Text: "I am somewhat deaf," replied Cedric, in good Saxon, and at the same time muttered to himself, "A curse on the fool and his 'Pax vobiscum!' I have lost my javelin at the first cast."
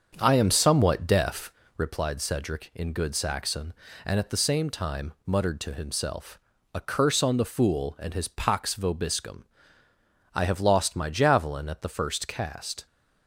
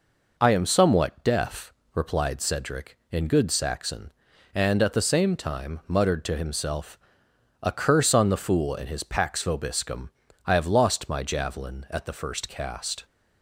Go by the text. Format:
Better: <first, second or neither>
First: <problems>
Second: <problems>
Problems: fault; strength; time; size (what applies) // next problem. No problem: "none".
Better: second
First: starts louder than the rest; until 2.0 s; 7 dB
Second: none